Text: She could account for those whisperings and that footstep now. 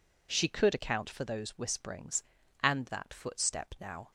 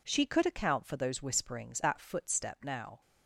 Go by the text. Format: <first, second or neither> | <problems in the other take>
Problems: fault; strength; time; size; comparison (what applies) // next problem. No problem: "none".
first | skips "and"; at 1.8 s